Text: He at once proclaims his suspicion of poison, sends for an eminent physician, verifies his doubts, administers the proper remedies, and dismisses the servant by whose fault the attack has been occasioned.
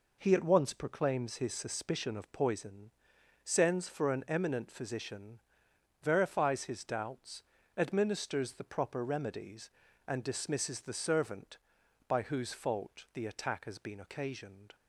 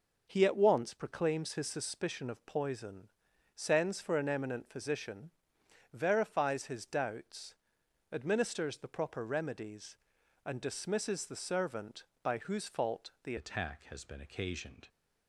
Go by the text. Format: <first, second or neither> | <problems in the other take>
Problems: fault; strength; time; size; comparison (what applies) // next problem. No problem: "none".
first | changes voice at "attack"; from 13.3 s on; 1.5 s long